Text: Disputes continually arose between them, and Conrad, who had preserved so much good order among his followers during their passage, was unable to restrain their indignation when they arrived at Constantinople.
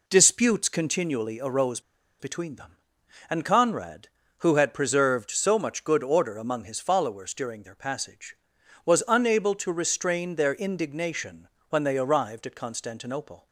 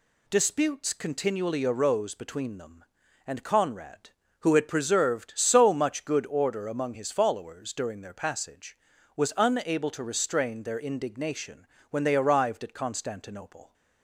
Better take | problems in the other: second | pauses between "arose" and "between"; at 1.7 s; 0.39 s long // pauses between "indignation" and "when"; slight; at 11.4 s; 0.22 s long; slight in the second

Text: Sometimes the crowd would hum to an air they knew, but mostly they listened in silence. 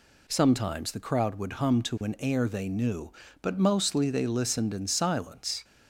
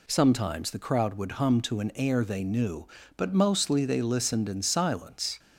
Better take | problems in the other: neither | none

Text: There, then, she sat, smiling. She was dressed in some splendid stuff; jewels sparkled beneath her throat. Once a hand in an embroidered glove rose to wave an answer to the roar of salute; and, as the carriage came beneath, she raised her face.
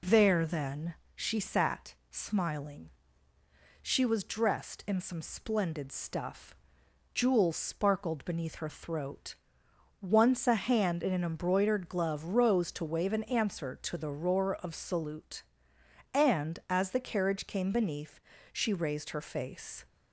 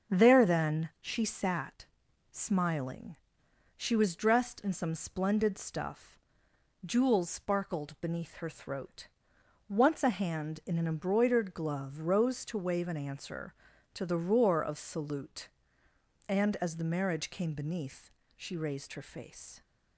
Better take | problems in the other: first | starts louder than the rest; until 1.2 s; 7 dB // says "marriage" for "carriage"; at 16.8 s

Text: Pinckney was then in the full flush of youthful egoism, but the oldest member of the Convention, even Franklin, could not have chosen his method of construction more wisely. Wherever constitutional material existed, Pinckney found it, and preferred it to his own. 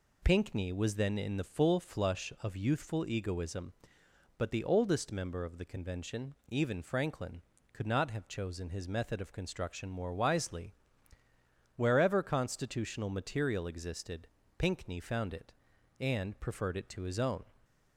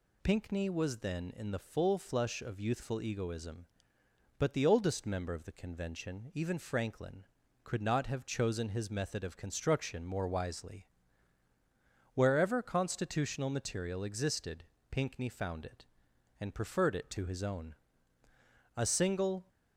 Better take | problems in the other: first | goes on to say "A single"; noticeable; from 18.7 s on; 0.72 s long

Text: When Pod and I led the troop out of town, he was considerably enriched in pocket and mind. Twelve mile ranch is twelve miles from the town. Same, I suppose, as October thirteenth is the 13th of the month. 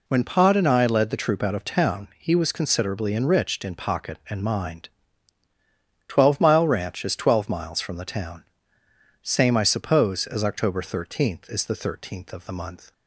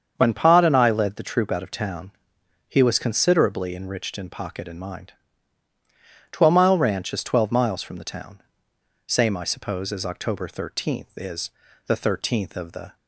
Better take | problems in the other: first | starts louder than the rest; strong; until 1.1 s; 7 dB // pauses between "is" and "the"; at 11.4 s; 0.38 s long // stops before "month"; at 12.9 s

